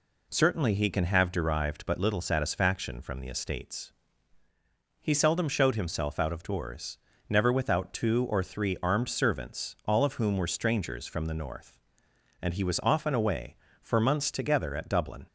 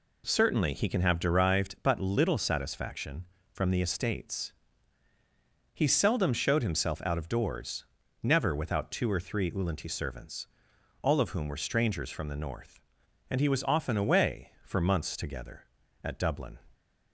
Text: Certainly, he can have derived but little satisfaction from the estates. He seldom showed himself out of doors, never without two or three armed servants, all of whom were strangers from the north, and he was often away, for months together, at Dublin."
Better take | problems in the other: first | says "ulanti" for "armed"; at 9.5 s

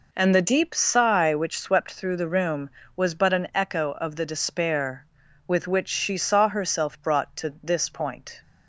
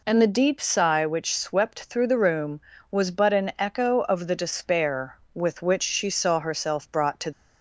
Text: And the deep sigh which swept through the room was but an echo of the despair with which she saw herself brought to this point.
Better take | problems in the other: first | stops before "this point"; at 7.3 s

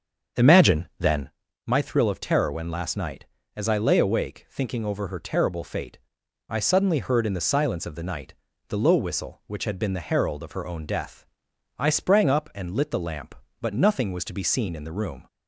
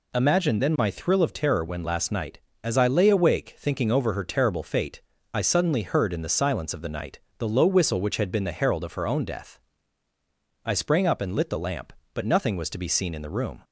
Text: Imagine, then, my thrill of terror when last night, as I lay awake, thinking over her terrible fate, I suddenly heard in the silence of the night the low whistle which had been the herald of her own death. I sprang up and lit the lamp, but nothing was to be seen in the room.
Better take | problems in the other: second | starts louder than the rest; strong; until 1.3 s; 7.5 dB // pauses between "night" and "the"; slight; at 8.3 s; 0.32 s long; slight in the second

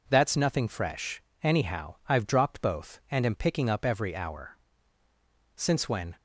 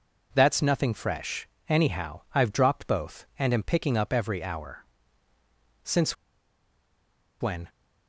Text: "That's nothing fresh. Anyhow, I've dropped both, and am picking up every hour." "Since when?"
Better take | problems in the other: first | pauses between "Since" and "when"; strong; at 6.1 s; 1.2 s long

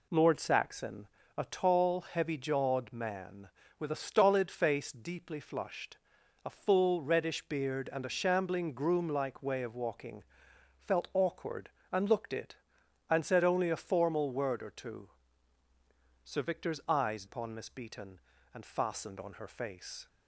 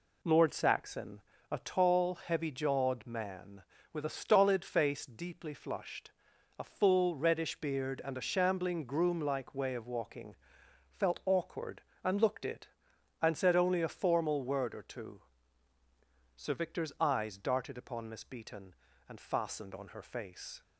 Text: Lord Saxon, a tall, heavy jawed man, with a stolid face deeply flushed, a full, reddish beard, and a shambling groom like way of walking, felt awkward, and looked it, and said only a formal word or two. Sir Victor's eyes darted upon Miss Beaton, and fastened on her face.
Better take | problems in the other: second | skips "darted"; at 17.2 s

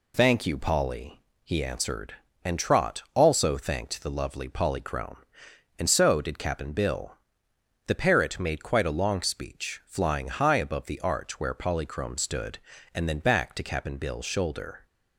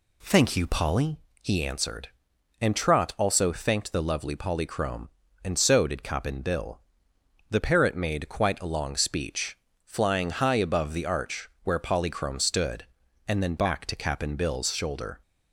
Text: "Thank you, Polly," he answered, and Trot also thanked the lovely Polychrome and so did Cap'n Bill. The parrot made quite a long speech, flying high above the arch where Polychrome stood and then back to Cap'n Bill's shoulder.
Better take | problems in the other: neither | none

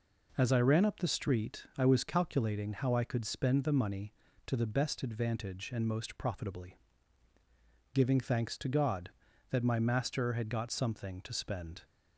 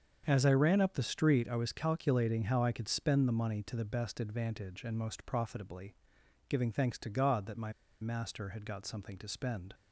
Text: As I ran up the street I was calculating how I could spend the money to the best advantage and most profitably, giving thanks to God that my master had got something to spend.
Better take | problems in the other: first | starts louder than the rest; until 1.2 s; 7 dB // pauses between "my" and "master"; slight; at 7.7 s; 0.30 s long

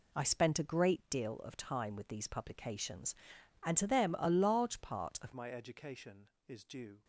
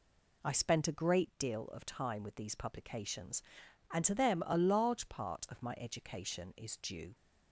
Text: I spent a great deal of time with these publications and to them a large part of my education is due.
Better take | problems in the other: second | changes voice at "my"; from 5.3 s on; 1.7 s long

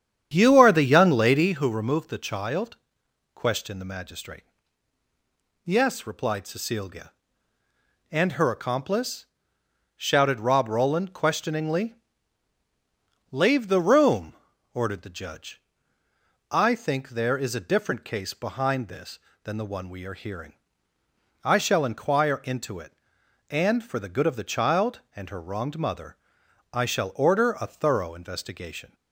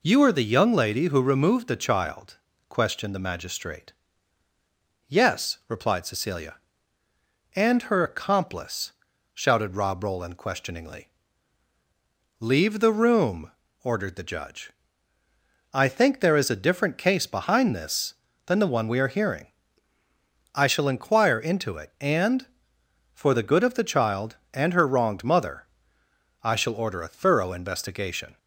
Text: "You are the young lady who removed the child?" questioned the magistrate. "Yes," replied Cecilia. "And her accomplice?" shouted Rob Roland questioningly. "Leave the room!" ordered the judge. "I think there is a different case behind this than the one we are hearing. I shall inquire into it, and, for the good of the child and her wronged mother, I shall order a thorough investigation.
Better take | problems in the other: second | starts louder than the rest; strong; until 1.7 s; 9 dB

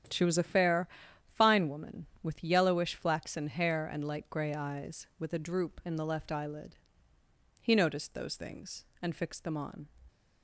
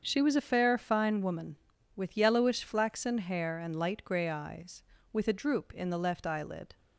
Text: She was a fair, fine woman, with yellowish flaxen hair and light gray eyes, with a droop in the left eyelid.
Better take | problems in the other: second | starts louder than the rest; strong; until 1.5 s; 9.5 dB; also in the second // goes on to say "He noticed those things and fixed them on"; strong; from 7.6 s on; 2.2 s long

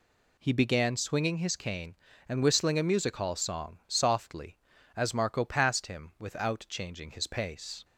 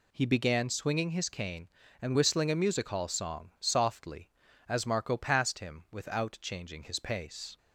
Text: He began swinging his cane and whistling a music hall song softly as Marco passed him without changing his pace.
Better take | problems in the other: neither | none

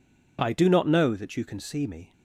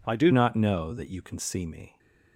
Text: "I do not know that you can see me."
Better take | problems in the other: first | changes voice at "not"; from 0.3 s on; 1.6 s long

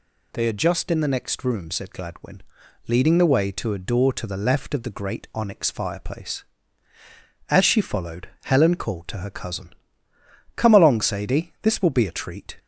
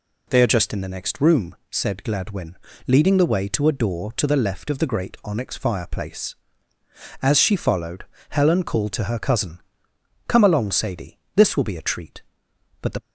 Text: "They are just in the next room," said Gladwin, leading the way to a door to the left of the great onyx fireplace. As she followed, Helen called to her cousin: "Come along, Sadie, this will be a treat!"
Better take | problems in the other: first | goes on to say "But the"; slight; from 12.8 s on; 0.20 s long

